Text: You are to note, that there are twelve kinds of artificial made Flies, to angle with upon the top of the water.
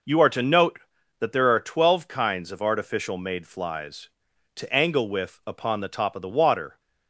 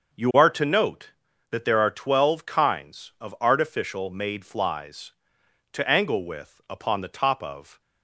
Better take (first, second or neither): first